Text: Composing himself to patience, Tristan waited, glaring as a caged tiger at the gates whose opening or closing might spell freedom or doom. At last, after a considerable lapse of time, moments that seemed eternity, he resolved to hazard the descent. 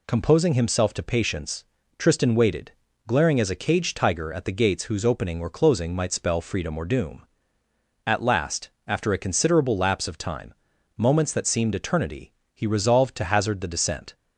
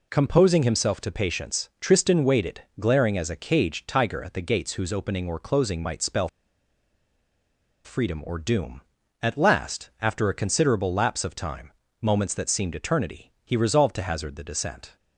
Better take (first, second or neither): first